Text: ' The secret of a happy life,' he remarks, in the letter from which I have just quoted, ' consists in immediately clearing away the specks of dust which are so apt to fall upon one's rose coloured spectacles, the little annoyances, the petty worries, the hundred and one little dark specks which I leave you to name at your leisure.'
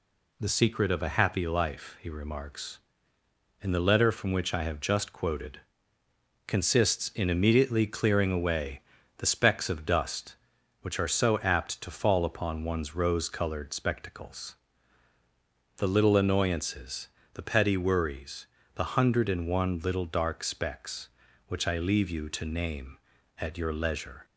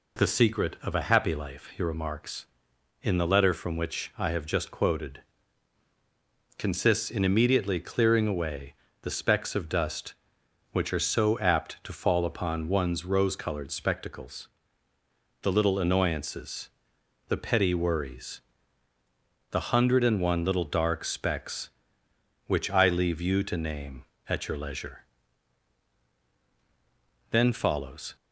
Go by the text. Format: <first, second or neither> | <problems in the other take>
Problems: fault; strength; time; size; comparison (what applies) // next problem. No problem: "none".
first | pauses between "away" and "the"; slight; at 8.7 s; 0.30 s long; also in the first // goes on to say "Then follows"; noticeable; from 27.2 s on; 0.86 s long